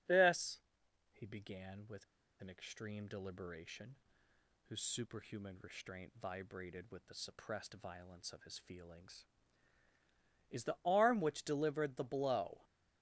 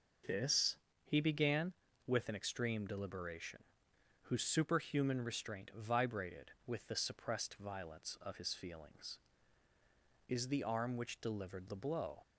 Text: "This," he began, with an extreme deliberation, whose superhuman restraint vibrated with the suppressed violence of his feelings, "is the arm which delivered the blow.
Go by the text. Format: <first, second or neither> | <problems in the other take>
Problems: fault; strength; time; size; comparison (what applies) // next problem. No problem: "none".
second | starts louder than the rest; strong; until 1.5 s; 7.5 dB // pauses between "with" and "an"; at 2.0 s; 0.37 s long